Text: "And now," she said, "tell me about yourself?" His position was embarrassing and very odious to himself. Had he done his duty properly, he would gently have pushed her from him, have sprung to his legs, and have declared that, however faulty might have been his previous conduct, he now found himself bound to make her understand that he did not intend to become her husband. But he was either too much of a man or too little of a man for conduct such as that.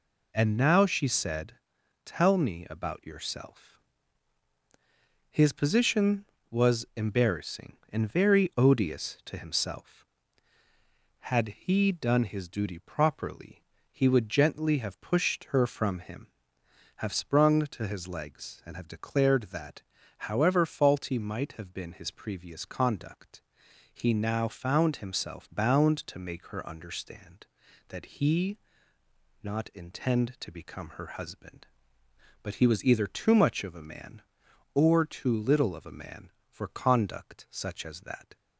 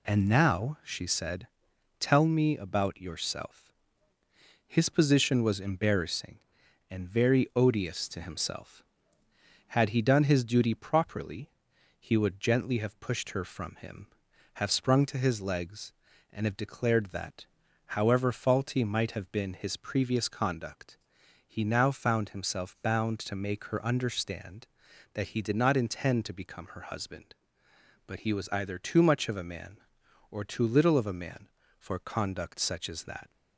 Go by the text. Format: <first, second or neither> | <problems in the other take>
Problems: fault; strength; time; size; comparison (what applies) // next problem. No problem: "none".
second | skips "did"; at 29.0 s